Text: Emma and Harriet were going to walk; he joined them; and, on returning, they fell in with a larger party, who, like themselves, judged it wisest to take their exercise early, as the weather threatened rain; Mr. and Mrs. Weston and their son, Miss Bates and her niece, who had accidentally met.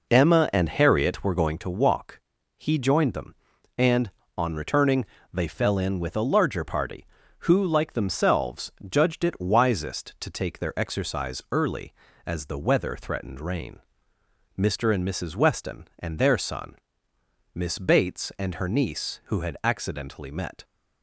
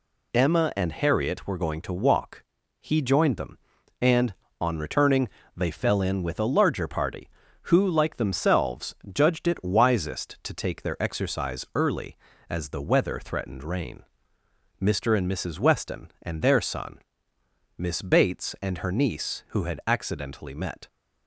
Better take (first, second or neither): second